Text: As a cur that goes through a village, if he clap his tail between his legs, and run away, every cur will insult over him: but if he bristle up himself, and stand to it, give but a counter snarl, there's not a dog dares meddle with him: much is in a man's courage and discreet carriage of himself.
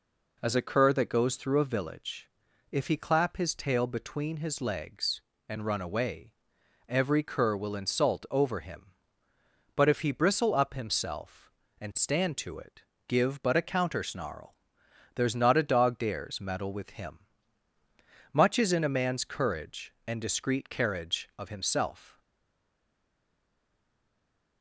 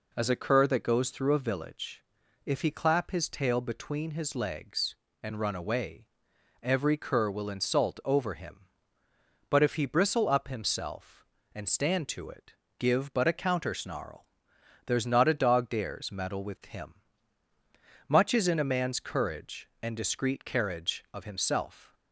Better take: second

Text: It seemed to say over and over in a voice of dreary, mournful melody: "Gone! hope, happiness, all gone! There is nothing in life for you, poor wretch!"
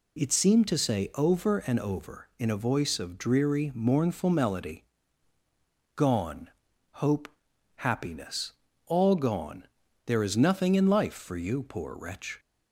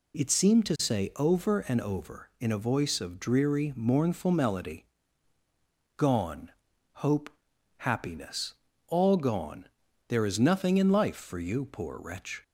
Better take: neither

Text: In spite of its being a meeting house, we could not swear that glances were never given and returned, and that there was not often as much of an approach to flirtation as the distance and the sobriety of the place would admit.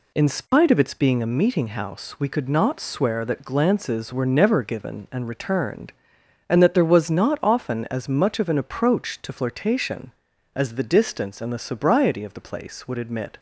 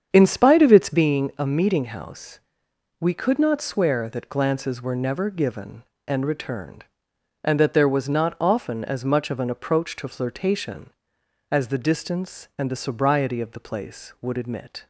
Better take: first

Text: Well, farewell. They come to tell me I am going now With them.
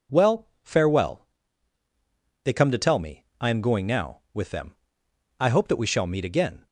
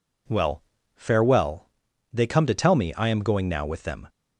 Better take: second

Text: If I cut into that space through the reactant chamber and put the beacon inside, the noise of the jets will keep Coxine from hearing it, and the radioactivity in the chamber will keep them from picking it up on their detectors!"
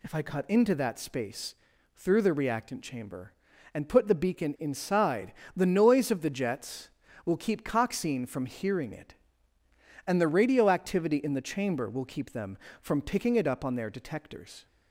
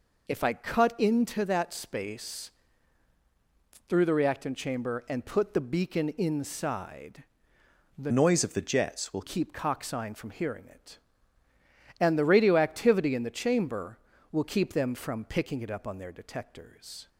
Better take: first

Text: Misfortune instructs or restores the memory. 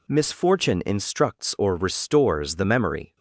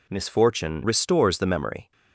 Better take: first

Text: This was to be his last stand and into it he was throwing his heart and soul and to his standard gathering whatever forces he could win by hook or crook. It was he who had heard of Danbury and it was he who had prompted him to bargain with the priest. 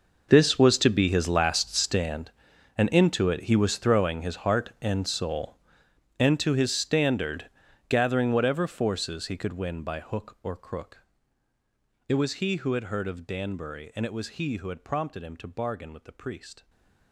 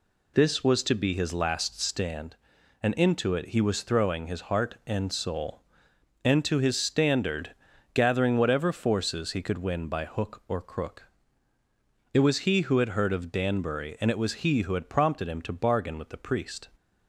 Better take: second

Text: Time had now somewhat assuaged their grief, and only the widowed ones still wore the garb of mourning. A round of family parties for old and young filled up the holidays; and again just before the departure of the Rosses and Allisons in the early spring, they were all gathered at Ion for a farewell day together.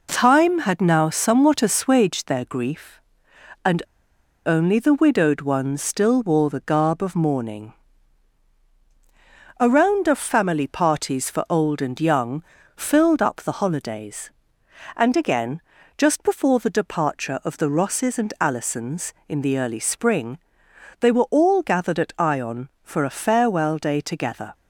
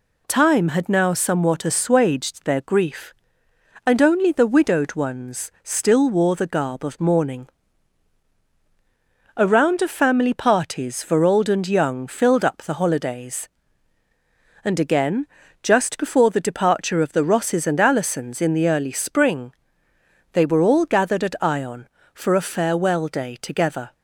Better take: second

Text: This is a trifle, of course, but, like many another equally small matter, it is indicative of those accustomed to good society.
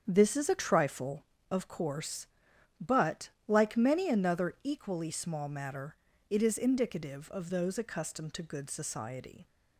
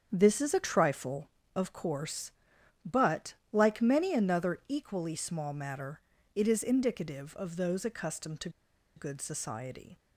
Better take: first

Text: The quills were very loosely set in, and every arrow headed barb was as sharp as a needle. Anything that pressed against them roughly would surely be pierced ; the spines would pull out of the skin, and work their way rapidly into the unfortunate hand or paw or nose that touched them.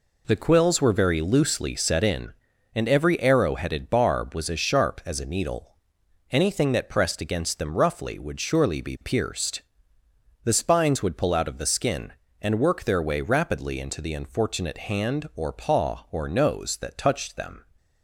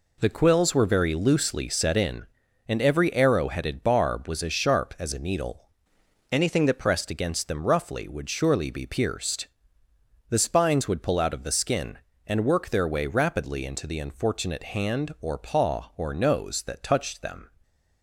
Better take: first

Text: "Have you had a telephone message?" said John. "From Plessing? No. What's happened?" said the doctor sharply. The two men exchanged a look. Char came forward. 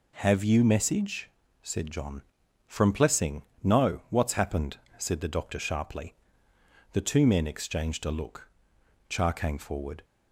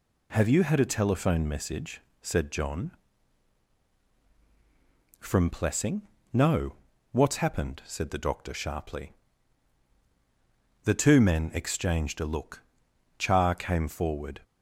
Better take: second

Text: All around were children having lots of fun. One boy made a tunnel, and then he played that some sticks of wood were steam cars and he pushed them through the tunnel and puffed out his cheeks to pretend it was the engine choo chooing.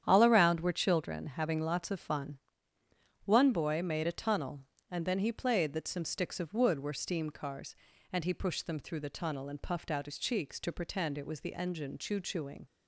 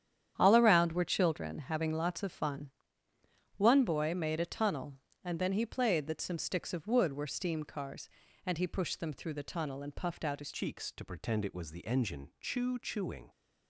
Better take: first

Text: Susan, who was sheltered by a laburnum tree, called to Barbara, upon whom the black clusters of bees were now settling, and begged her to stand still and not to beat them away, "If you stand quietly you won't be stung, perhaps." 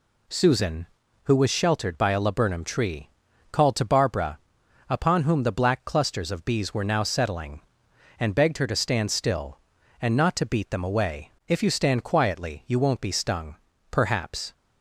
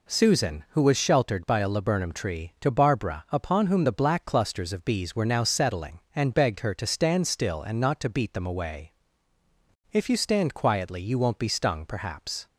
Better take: first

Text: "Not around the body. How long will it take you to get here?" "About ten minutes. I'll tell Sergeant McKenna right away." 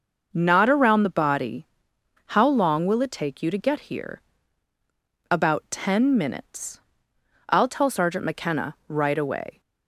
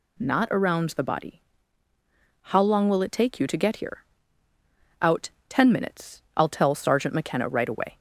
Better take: first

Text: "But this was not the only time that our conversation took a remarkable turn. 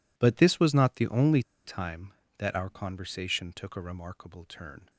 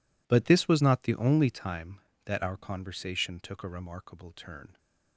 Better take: second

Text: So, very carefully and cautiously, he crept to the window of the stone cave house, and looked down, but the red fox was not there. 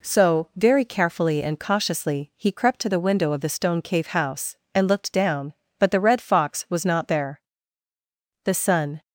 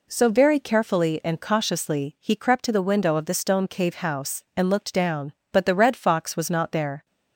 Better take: second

